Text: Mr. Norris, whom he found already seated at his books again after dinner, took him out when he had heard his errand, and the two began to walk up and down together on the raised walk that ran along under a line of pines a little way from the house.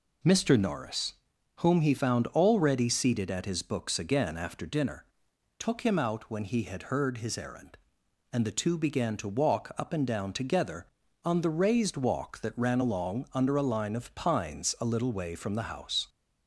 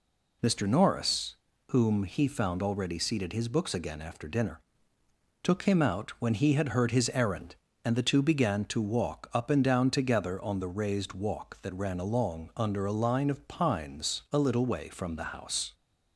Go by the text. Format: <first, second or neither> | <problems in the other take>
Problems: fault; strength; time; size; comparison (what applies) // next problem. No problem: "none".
first | skips "at"; at 3.3 s